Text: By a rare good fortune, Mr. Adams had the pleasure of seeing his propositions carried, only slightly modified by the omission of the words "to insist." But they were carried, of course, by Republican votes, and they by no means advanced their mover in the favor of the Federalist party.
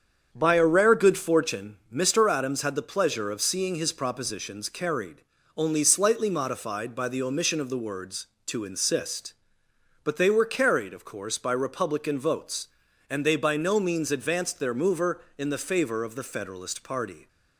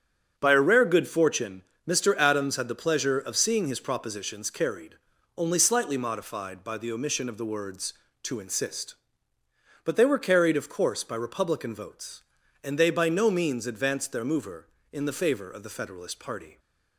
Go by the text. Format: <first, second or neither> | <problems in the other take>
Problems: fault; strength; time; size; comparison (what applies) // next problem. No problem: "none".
neither | starts louder than the rest; strong; the same in both